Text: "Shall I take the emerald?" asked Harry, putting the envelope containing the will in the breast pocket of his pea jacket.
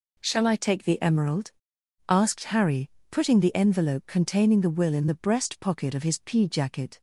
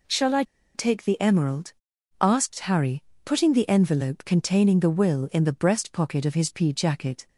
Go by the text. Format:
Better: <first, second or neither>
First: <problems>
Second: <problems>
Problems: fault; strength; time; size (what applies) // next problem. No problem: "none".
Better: first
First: none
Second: pauses between "I" and "take"; slight; at 0.4 s; 0.32 s long